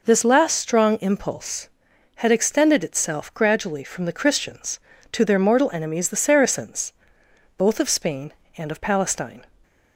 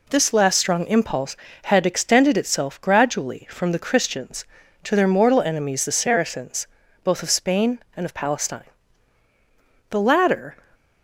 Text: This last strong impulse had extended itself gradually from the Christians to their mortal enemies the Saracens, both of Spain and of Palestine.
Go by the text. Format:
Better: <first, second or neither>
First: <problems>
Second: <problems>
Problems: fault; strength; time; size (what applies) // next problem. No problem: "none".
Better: first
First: none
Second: goes on to say "The latter"; noticeable; from 9.9 s on; 0.66 s long